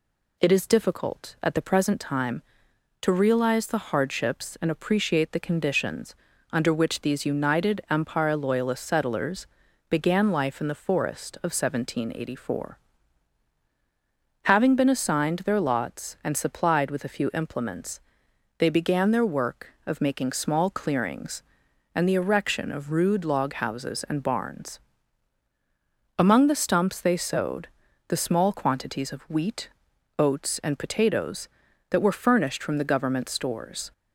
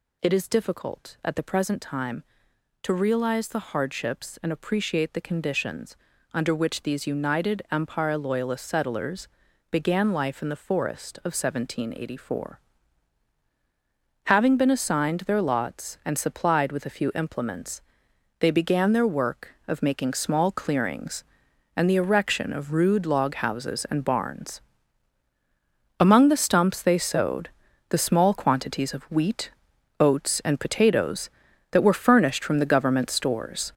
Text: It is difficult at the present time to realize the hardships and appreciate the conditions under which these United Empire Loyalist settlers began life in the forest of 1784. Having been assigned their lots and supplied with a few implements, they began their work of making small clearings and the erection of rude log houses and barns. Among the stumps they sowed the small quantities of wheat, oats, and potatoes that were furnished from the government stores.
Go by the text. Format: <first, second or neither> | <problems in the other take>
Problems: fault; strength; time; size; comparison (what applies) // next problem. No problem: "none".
first | gets louder; throughout; 6.5 dB // pauses between "conditions" and "under"; at 5.9 s; 0.38 s long; also in the first // pauses between "settlers" and "began"; at 9.2 s; 0.42 s long; also in the first // pauses between "sowed" and "the"; at 27.4 s; 0.40 s long; also in the first